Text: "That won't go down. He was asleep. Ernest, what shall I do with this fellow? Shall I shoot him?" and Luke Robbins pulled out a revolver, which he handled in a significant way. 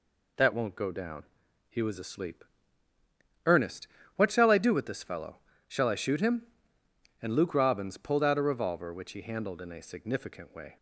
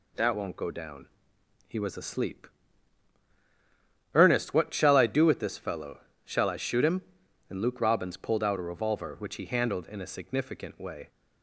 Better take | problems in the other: neither | none

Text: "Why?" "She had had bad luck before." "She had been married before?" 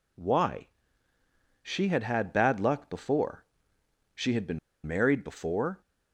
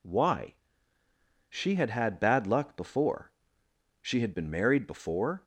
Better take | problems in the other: second | pauses between "been" and "married"; slight; at 4.5 s; 0.27 s long

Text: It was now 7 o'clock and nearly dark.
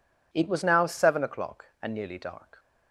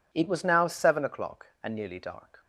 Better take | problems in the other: neither | none

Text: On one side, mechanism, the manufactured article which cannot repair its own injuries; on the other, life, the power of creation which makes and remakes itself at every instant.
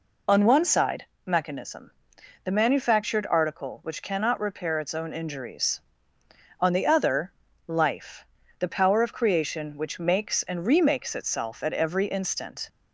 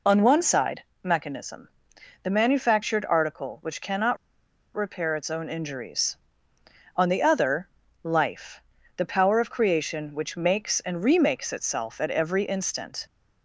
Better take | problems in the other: first | pauses between "cannot" and "repair"; noticeable; at 4.1 s; 0.58 s long

